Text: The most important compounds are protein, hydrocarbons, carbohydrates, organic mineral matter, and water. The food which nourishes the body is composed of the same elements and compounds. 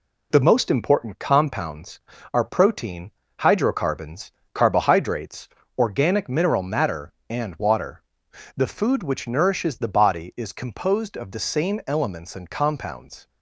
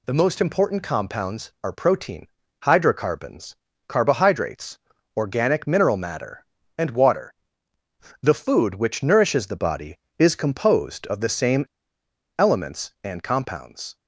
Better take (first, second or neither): first